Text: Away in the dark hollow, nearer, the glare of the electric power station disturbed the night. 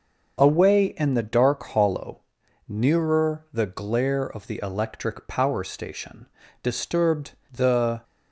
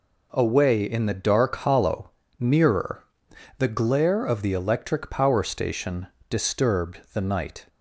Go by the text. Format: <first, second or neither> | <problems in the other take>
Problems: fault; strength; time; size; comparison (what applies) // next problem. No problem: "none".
second | starts louder than the rest; until 1.4 s; 6.5 dB // pauses between "station" and "disturbed"; slight; at 6.2 s; 0.36 s long; slight in the second // pauses between "disturbed" and "the"; slight; at 7.3 s; 0.18 s long // stops before "night"; at 8.0 s